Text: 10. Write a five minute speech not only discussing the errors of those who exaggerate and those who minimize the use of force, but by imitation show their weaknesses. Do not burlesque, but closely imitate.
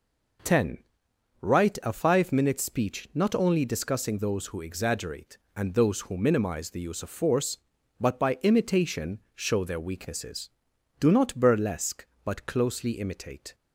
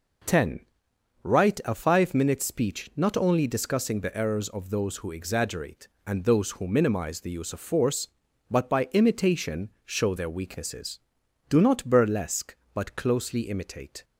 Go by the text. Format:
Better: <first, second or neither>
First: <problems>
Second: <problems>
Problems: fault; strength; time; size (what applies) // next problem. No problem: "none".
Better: second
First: skips "the errors of"; at 4.1 s // pauses between "imitation" and "show"; slight; at 9.1 s; 0.16 s long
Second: pauses between "imitation" and "show"; slight; at 9.6 s; 0.16 s long